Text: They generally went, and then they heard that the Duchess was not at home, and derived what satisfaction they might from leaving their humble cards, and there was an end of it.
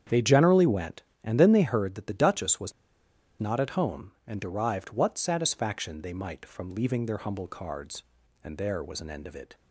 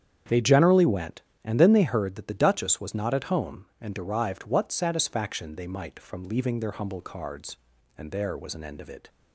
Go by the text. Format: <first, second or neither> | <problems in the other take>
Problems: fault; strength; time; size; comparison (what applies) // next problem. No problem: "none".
second | starts louder than the rest; strong; until 1.3 s; 8.5 dB; strong in the second // pauses between "was" and "not"; noticeable; at 2.7 s; 0.67 s long